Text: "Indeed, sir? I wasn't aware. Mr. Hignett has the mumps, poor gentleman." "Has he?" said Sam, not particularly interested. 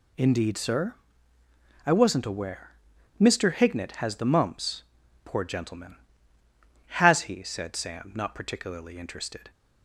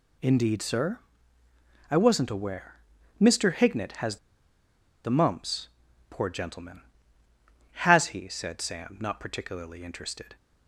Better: first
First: none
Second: pauses between "has" and "the"; noticeable; at 4.1 s; 0.87 s long

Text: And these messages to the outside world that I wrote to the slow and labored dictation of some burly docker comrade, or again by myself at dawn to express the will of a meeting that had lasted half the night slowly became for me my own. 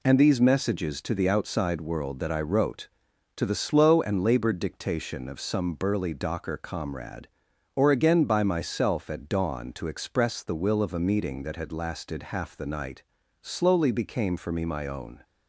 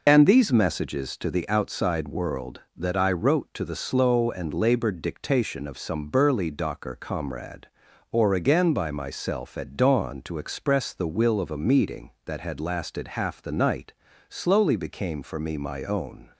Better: first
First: pauses between "night" and "slowly"; at 13.0 s; 0.38 s long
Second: loses the start of "And"; at 0.0 s; 45 ms // pauses between "night" and "slowly"; slight; at 13.9 s; 0.34 s long

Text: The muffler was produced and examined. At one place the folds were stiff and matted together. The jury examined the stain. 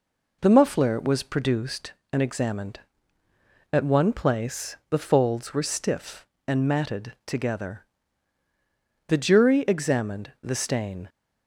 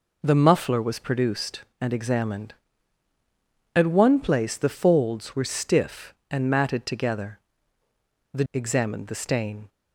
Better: first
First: none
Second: skips "jury"; at 8.4 s

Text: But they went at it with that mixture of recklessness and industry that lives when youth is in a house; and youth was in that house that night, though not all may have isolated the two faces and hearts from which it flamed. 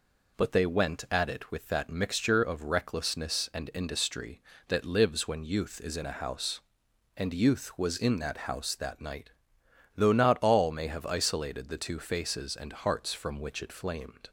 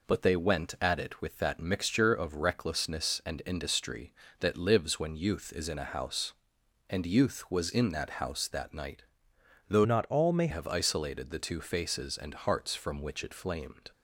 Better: first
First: none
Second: changes voice from "not" to "may"; from 9.8 to 10.4 s; 0.6 s long

